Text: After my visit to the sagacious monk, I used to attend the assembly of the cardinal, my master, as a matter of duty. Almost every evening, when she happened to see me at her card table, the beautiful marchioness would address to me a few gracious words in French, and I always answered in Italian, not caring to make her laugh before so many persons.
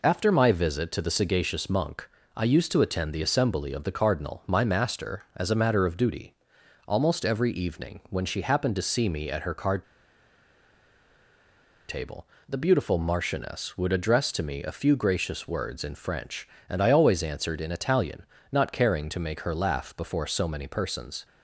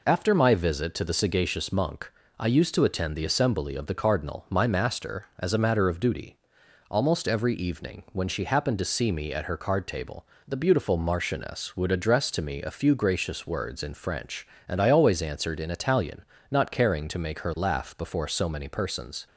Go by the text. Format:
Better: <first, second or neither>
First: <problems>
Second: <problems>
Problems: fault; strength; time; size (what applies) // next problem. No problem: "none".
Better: second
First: pauses between "card" and "table"; strong; at 9.8 s; 2.0 s long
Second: none